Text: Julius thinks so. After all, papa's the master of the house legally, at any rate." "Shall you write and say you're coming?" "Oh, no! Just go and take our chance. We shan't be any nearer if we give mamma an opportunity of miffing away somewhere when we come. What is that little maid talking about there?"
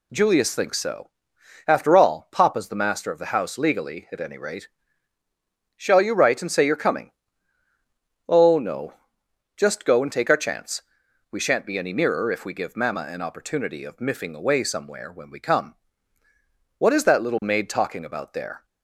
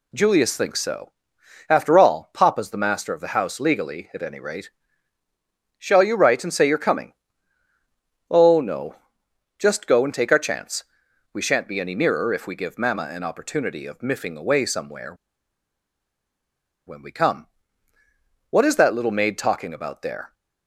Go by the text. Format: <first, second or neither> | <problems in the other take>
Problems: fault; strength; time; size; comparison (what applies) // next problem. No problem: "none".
first | pauses between "somewhere" and "when"; strong; at 15.1 s; 1.7 s long